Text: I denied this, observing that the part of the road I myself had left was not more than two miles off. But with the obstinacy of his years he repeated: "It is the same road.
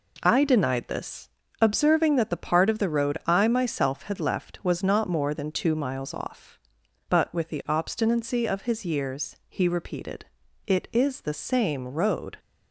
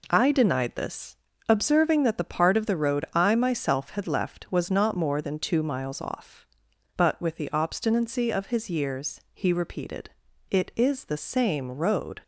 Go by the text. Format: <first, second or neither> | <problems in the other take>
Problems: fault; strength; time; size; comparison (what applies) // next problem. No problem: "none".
neither | none